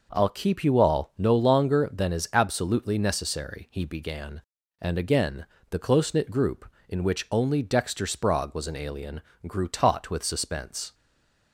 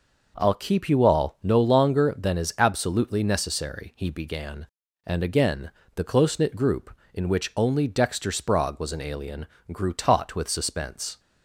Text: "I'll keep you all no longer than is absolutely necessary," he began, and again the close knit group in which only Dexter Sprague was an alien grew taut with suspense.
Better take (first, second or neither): second